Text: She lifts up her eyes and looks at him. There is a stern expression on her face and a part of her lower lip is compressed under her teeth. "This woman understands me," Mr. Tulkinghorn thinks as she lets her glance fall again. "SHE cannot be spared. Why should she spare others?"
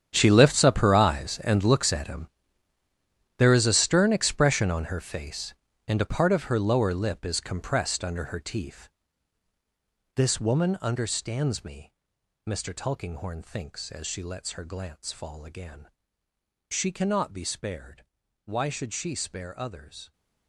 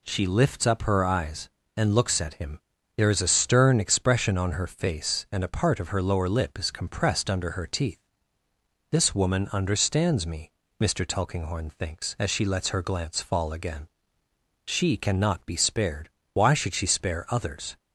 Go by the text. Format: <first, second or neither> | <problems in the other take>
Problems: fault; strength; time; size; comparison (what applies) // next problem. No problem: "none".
second | gets quieter; strong; throughout; 16.5 dB